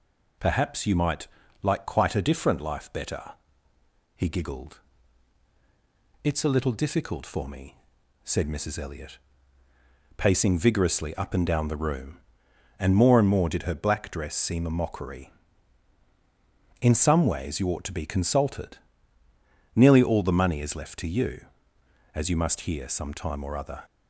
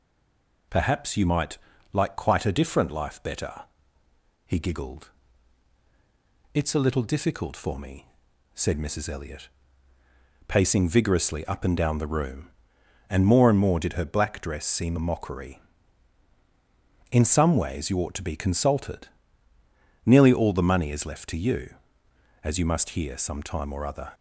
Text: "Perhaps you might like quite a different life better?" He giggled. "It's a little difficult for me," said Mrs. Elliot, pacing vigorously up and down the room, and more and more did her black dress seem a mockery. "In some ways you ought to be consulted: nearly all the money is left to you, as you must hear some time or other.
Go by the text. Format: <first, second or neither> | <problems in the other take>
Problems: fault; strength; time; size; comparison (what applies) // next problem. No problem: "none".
first | stays silent before the first word; slight; until 0.7 s; 0.7 s long // pauses between "might" and "like"; slight; at 1.5 s; 0.34 s long; slight in the first